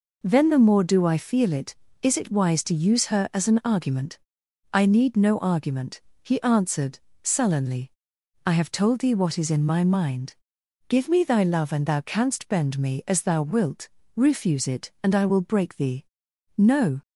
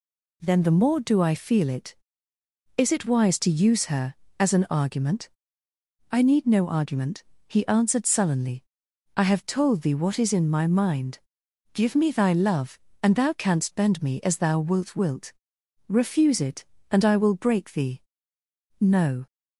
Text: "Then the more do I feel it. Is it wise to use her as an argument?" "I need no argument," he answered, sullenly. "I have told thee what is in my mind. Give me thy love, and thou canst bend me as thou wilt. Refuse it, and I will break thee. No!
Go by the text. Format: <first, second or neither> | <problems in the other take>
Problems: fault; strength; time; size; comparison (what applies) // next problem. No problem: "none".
first | says "wilt" twice; at 14.9 s